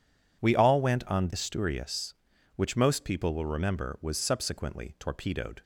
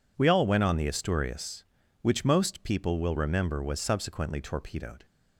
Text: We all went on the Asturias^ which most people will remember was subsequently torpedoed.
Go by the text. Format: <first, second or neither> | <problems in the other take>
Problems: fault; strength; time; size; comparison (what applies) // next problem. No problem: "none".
second | skips "the"; at 1.3 s